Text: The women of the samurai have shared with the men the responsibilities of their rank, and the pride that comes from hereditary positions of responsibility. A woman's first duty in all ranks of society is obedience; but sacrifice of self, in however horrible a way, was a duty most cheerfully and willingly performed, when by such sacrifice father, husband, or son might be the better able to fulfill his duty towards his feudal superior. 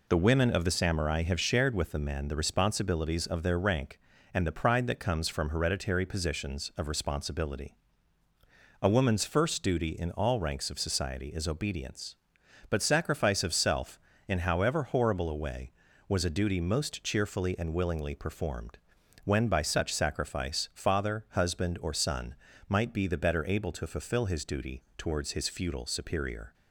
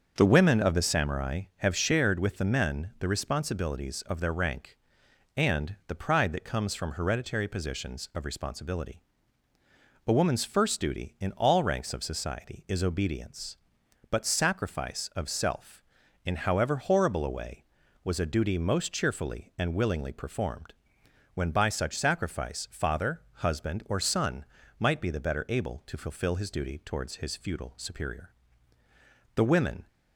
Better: first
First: pauses between "son" and "might"; slight; at 22.3 s; 0.36 s long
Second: starts louder than the rest; until 1.1 s; 6.5 dB // pauses between "son" and "might"; slight; at 24.4 s; 0.34 s long // goes on to say "The women"; from 29.3 s on; 0.52 s long

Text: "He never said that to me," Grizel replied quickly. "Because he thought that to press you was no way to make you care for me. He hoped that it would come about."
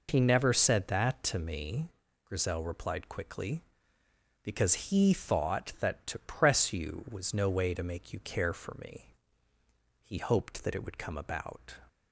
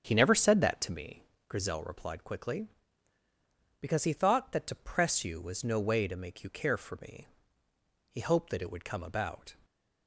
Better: first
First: none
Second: starts louder than the rest; strong; until 1.7 s; 7.5 dB // stays silent after the last word; slight; from 9.5 s on; 0.5 s long

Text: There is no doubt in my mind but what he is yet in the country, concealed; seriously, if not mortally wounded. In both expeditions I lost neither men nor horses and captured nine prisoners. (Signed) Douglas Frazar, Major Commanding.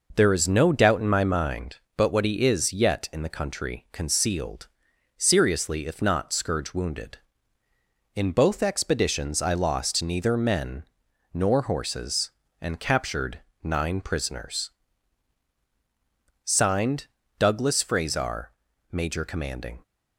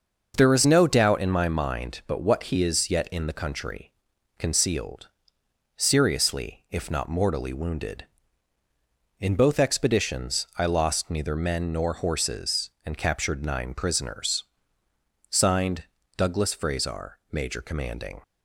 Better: second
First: says "scourge" for "mortally"; at 6.3 s // pauses between "men" and "nor"; noticeable; at 10.8 s; 0.50 s long // pauses between "captured" and "nine"; slight; at 13.4 s; 0.22 s long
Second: none

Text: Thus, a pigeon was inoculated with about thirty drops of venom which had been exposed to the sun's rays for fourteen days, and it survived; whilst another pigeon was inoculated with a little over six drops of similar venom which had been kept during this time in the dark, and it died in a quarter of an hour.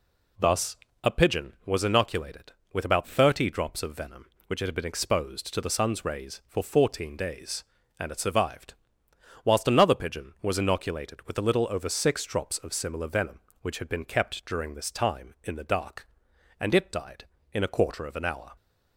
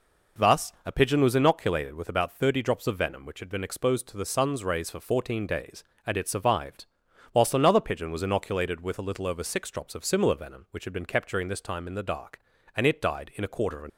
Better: first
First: none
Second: stops before "hour"; at 13.8 s

